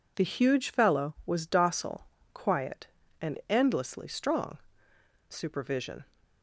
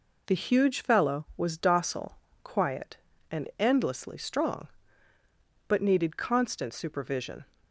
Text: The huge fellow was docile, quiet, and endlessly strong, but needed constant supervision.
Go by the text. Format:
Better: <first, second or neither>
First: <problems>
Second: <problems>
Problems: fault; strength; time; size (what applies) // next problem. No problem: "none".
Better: second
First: skips "but needed constant"; at 4.9 s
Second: none